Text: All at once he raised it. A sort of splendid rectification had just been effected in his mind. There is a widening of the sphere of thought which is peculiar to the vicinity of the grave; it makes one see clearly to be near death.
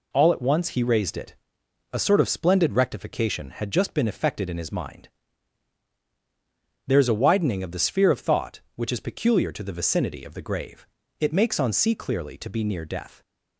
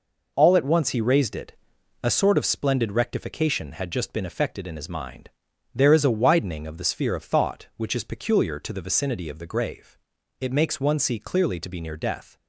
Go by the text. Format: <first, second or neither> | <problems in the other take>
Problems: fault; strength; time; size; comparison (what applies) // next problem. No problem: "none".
second | says "on" for "one"; at 11.5 s